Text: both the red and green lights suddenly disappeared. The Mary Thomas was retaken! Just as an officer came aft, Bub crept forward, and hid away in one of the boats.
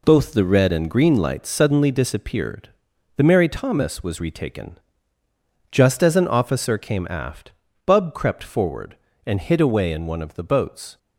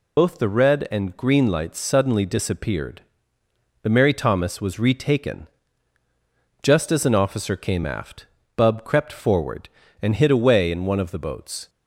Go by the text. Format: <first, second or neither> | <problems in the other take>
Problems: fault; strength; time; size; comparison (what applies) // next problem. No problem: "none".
first | loses the start of "both"; at 0.1 s; 60 ms